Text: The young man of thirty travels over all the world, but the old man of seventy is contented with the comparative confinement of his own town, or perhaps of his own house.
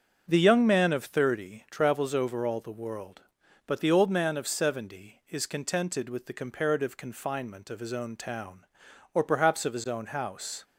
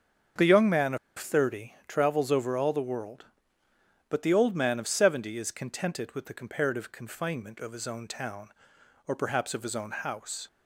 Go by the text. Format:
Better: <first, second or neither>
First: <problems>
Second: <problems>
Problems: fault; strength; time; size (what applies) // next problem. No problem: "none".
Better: first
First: starts louder than the rest; until 1.2 s; 7 dB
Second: starts louder than the rest; until 1.5 s; 7 dB // pauses between "of" and "thirty"; slight; at 0.9 s; 0.20 s long